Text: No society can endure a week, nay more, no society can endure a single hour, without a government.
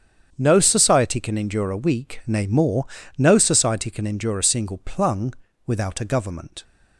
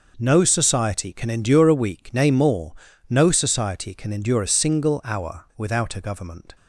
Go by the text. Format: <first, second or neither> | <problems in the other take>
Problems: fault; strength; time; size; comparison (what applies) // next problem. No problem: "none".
second | starts louder than the rest; strong; until 1.3 s; 8.5 dB // says "plung" for "hour"; at 4.7 s